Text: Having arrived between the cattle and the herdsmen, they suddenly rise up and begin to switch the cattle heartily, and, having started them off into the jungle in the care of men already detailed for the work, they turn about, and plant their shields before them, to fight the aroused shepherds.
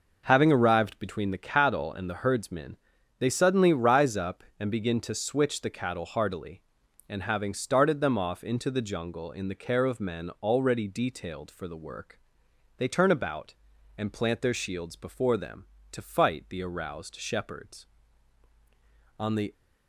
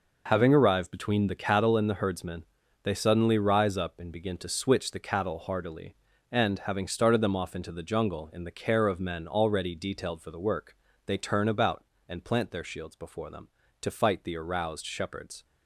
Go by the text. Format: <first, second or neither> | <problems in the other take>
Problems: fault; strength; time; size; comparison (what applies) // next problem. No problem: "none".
second | goes on to say "On the"; slight; from 19.1 s on; 0.34 s long